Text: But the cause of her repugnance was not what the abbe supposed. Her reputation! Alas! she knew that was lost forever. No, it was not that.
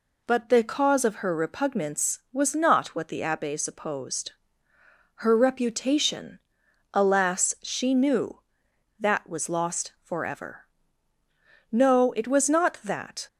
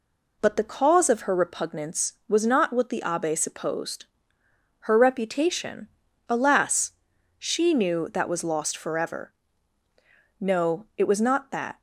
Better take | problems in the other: neither | none

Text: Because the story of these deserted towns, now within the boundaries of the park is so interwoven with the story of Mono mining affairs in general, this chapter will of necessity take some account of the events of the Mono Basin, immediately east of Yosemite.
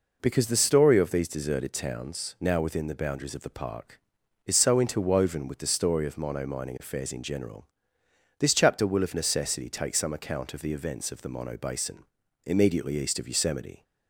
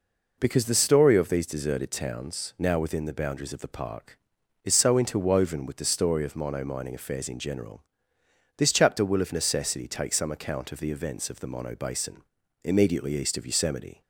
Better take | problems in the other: neither | none

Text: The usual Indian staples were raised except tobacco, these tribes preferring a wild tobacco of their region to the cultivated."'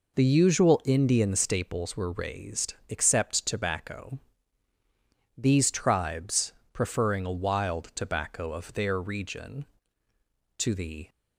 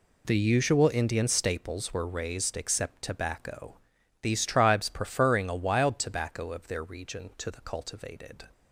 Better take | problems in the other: second | pauses between "tribes" and "preferring"; slight; at 6.5 s; 0.20 s long // stops before "cultivated"; at 11.0 s

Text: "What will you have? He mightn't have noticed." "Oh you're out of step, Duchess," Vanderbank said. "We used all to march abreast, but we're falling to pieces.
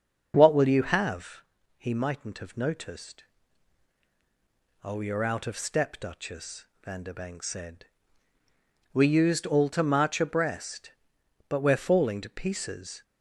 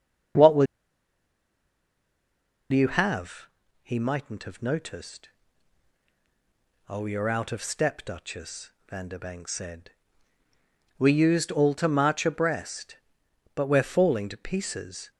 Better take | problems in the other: first | starts louder than the rest; until 3.4 s; 6.5 dB; also in the first // pauses between "will" and "you"; strong; at 0.6 s; 2.0 s long

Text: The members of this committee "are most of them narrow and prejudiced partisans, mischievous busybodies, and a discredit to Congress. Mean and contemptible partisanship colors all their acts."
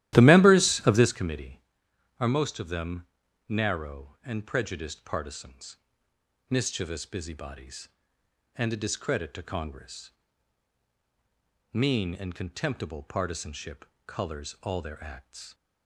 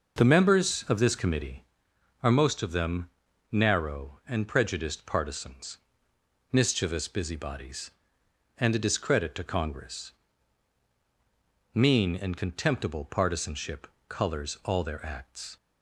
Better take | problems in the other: second | starts louder than the rest; strong; until 1.1 s; 14 dB // pauses between "them" and "narrow"; at 3.0 s; 0.44 s long; also in the second // pauses between "partisanship" and "colors"; slight; at 13.8 s; 0.20 s long; slight in the second

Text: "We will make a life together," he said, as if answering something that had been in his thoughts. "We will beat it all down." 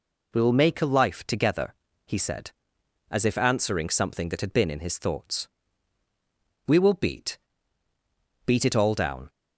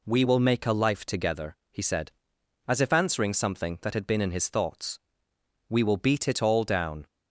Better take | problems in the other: second | says "beat" twice; at 8.4 s

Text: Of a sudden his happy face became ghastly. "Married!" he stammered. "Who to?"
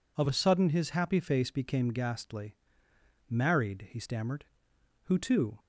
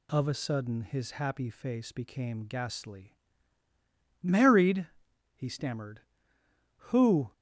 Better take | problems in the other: first | stops before "to"; at 7.3 s

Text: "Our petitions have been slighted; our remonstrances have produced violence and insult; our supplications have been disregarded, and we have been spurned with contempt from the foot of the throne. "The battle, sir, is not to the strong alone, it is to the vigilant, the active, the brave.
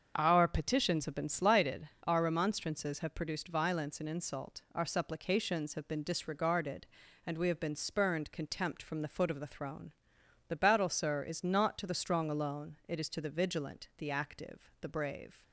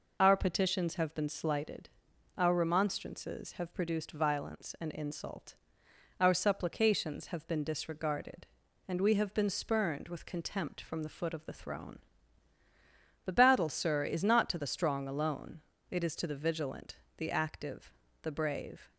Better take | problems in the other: second | starts louder than the rest; until 1.1 s; 7 dB // skips "with"; at 8.3 s

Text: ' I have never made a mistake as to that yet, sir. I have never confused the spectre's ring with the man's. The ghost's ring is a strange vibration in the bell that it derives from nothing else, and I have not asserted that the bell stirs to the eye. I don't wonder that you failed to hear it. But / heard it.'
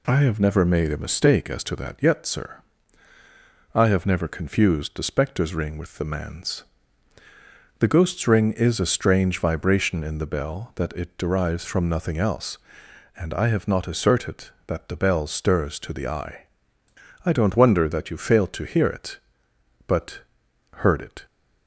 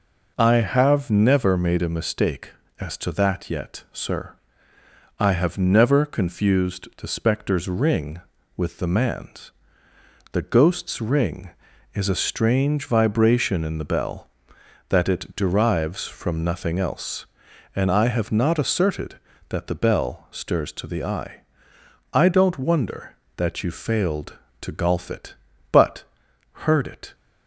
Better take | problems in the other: first | says "golf" for "hear"; at 24.7 s

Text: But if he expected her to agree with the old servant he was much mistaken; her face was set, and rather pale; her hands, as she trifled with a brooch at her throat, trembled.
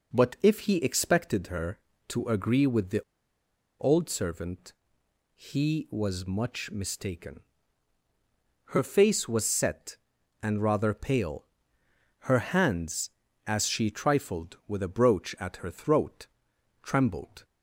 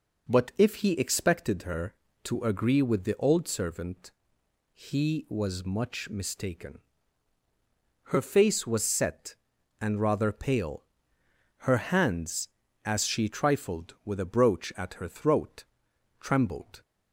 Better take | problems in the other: second | pauses between "the" and "old"; noticeable; at 3.0 s; 0.79 s long // pauses between "servant" and "he"; noticeable; at 4.7 s; 0.64 s long; noticeable in the second

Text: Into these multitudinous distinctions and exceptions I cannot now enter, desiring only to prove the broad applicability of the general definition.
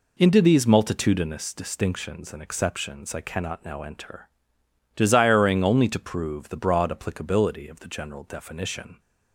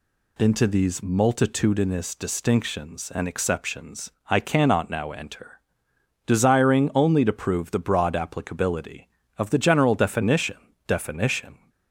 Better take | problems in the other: first | pauses between "exceptions" and "I"; slight; at 4.1 s; 0.18 s long // says "definition" twice; at 10.8 s

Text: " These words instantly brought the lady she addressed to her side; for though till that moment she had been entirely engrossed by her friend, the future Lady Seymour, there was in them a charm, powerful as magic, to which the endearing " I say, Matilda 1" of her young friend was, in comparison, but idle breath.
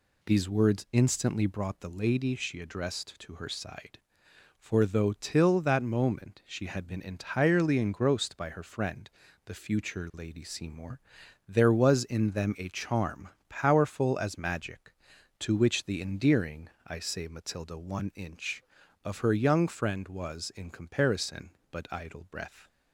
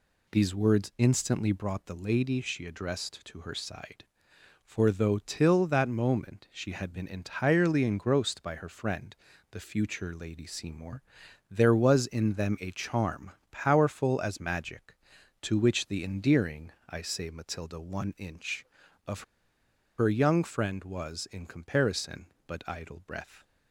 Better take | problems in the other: first | pauses between "of" and "her"; noticeable; at 19.2 s; 0.75 s long

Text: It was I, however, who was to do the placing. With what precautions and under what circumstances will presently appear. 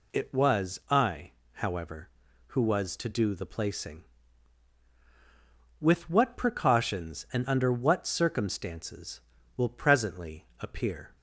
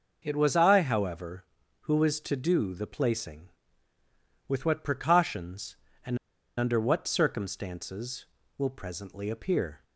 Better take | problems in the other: first | pauses between "and" and "under"; at 6.1 s; 0.40 s long

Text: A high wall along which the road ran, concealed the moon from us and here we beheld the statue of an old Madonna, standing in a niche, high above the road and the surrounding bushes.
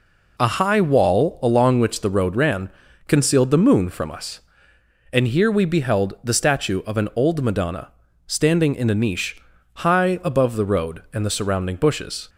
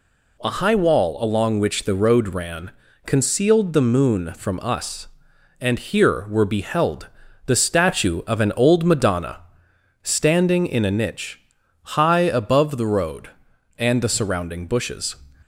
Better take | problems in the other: first | says "were" for "we"; at 6.2 s // pauses between "beheld" and "the"; at 7.0 s; 0.40 s long

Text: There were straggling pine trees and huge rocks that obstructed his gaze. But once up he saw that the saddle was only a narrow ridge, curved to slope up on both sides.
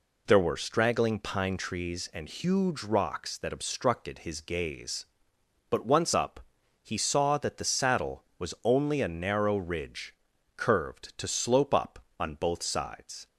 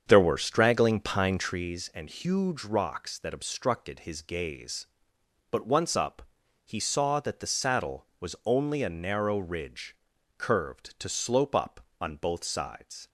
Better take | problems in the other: first | starts louder than the rest; strong; until 1.7 s; 7.5 dB // pauses between "up" and "he"; at 6.2 s; 0.42 s long; also in the first

